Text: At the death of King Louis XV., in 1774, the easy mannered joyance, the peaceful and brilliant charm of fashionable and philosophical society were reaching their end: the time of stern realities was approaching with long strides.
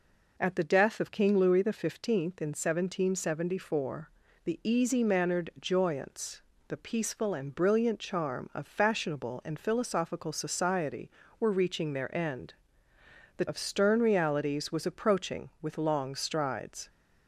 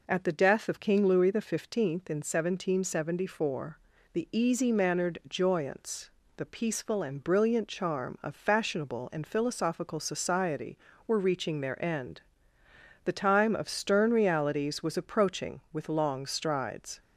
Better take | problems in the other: second | skips "time"; at 13.4 s

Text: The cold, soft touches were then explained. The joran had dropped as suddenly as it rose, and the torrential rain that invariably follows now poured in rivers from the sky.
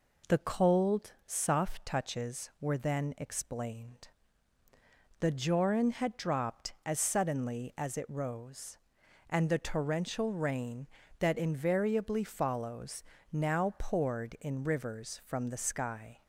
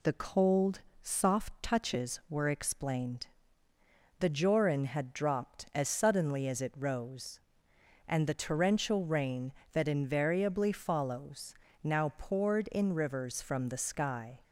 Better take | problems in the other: first | skips "then"; at 2.4 s // pauses between "follows" and "now"; slight; at 11.5 s; 0.30 s long; slight in the first

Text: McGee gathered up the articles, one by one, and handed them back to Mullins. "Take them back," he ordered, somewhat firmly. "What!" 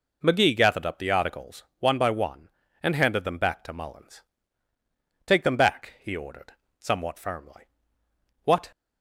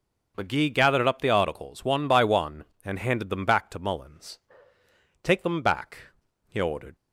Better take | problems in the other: first | stops before "somewhat firmly What"; at 6.9 s

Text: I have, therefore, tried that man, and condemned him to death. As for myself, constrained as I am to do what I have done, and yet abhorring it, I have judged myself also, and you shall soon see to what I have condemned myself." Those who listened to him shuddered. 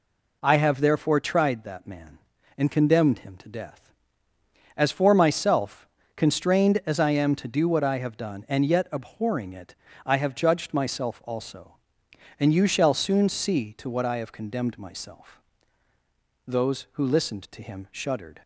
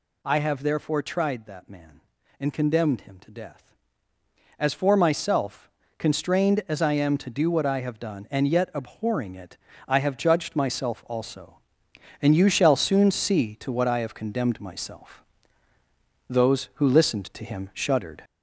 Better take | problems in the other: first | gets louder; noticeable; throughout; 4.5 dB

